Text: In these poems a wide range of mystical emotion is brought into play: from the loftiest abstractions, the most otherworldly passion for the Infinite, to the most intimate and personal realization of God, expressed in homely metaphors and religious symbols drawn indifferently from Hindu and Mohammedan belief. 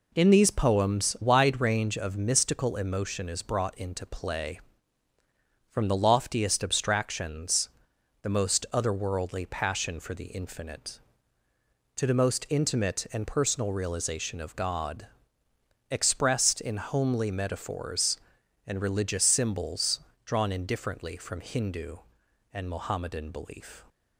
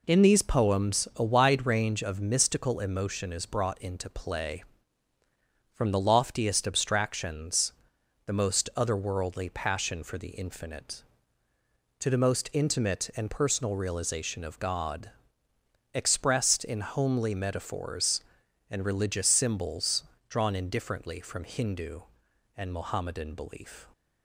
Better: second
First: skips "a"; at 1.1 s // pauses between "symbols" and "drawn"; slight; at 19.9 s; 0.26 s long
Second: pauses between "symbols" and "drawn"; slight; at 20.0 s; 0.26 s long

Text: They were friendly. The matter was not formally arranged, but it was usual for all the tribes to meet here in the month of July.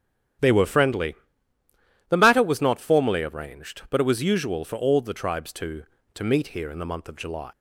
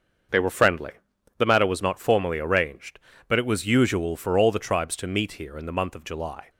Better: second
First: starts louder than the rest; strong; until 2.3 s; 10.5 dB // says "to" twice; at 6.1 s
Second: starts louder than the rest; until 1.7 s; 6.5 dB

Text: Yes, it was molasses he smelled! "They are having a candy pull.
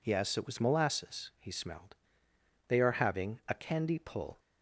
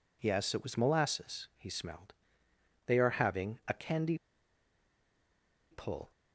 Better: first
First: none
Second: pauses between "candy" and "pull"; strong; at 4.1 s; 1.5 s long

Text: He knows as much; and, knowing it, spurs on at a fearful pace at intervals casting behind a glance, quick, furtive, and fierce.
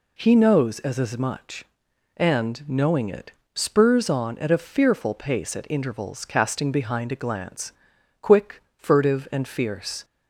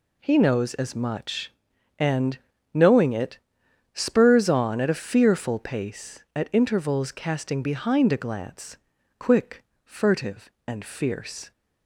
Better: second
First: says "as" twice; at 0.9 s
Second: none

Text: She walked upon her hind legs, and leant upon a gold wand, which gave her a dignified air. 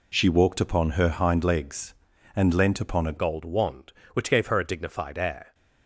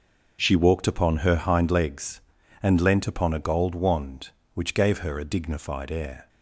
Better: second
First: changes voice at "gold"; from 3.1 s on; 2.4 s long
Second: none

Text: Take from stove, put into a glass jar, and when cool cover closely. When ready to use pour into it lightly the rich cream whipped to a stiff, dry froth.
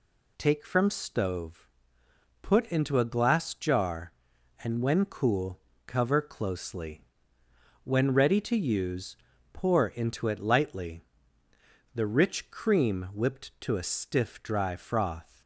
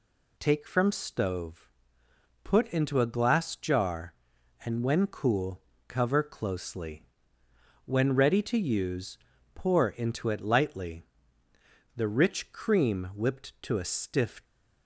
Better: first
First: pauses between "cool" and "cover"; slight; at 5.6 s; 0.26 s long // pauses between "use" and "pour"; at 9.1 s; 0.38 s long // pauses between "lightly" and "the"; noticeable; at 11.0 s; 0.92 s long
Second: pauses between "cool" and "cover"; slight; at 5.6 s; 0.26 s long // pauses between "use" and "pour"; at 9.1 s; 0.38 s long // pauses between "lightly" and "the"; noticeable; at 11.0 s; 0.92 s long // stops before "dry froth"; at 14.4 s

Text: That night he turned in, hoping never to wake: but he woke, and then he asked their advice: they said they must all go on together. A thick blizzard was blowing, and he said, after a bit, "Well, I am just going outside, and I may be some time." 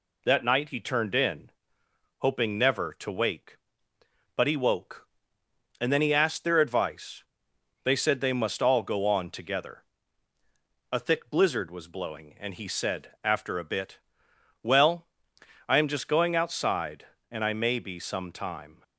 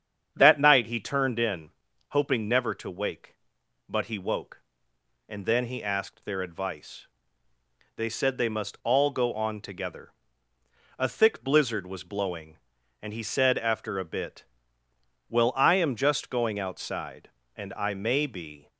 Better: first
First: none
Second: starts louder than the rest; strong; until 1.3 s; 8 dB // stops before "some time"; at 18.6 s

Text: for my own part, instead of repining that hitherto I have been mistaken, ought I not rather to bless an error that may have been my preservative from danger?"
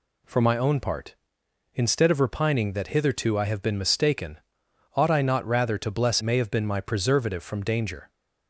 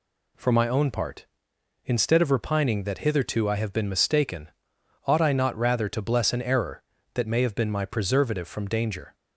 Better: second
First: skips "an error that"; at 6.2 s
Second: none

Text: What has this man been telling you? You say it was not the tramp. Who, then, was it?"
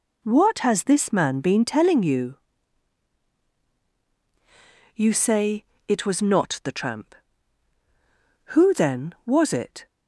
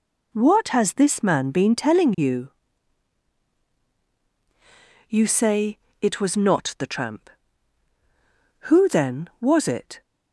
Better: neither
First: pauses between "say" and "it"; slight; at 5.6 s; 0.24 s long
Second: pauses between "say" and "it"; slight; at 5.7 s; 0.24 s long

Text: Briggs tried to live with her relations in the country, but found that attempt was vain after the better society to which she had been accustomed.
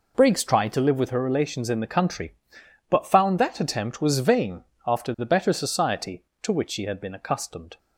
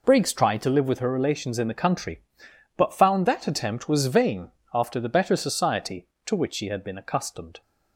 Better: neither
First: pauses between "vain" and "after"; slight; at 4.6 s; 0.22 s long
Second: pauses between "vain" and "after"; slight; at 4.5 s; 0.22 s long

